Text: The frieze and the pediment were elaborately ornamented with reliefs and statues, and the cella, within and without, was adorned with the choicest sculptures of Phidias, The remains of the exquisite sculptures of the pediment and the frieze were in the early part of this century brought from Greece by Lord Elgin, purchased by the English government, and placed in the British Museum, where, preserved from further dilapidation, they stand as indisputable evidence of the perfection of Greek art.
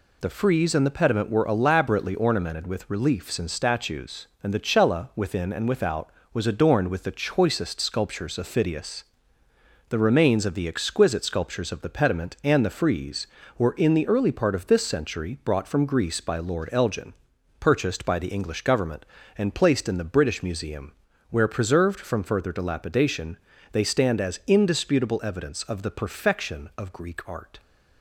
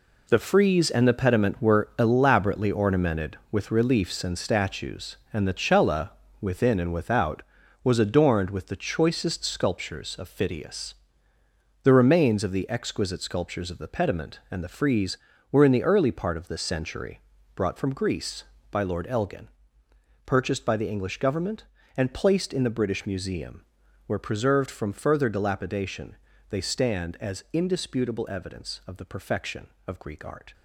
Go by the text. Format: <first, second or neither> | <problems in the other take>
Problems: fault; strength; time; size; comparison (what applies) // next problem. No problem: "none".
first | gets quieter; strong; throughout; 9.5 dB // pauses between "century" and "brought"; slight; at 17.2 s; 0.34 s long